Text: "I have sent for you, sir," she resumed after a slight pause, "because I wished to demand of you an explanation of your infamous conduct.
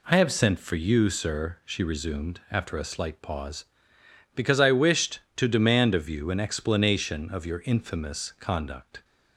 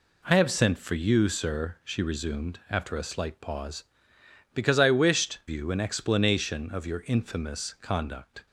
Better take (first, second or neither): first